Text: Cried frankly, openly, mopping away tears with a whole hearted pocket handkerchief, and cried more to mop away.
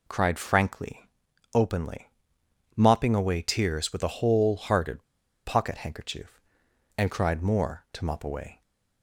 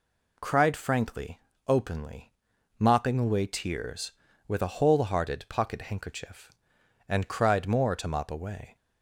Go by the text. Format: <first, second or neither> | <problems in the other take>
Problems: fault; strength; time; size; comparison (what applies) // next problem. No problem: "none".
second | pauses between "hearted" and "pocket"; at 5.0 s; 0.42 s long